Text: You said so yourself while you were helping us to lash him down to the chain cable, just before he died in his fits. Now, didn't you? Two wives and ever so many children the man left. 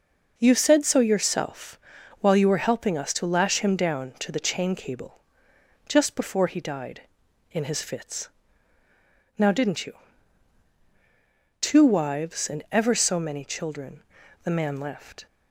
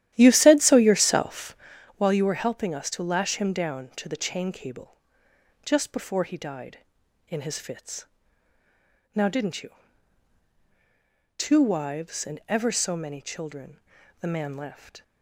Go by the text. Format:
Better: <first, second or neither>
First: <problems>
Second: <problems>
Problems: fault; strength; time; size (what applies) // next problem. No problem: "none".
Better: first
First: pauses between "yourself" and "while"; at 1.7 s; 0.42 s long // pauses between "children" and "the"; at 14.0 s; 0.42 s long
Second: starts louder than the rest; strong; until 1.8 s; 12.5 dB // pauses between "yourself" and "while"; at 1.5 s; 0.42 s long // pauses between "children" and "the"; at 13.7 s; 0.42 s long